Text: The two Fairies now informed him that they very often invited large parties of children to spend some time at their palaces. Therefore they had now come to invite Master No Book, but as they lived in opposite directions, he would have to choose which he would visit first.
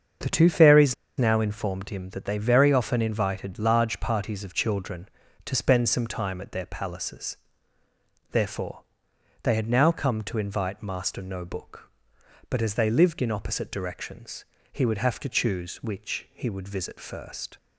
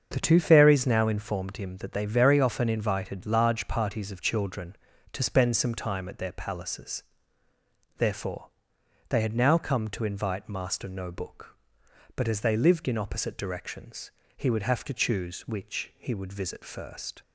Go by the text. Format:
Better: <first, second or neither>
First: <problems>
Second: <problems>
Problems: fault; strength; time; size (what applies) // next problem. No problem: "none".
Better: second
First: starts louder than the rest; until 1.4 s; 7 dB // pauses between "Fairies" and "now"; slight; at 0.9 s; 0.24 s long // pauses between "Therefore" and "they"; noticeable; at 8.8 s; 0.58 s long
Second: starts louder than the rest; until 1.1 s; 7 dB // pauses between "Therefore" and "they"; noticeable; at 8.4 s; 0.58 s long